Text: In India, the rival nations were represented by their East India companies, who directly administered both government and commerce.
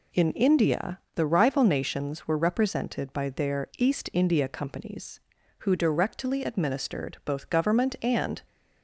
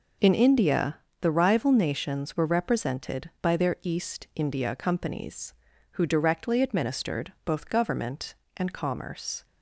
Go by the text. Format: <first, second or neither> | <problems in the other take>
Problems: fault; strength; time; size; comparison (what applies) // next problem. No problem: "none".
second | stops before "commerce"; at 8.4 s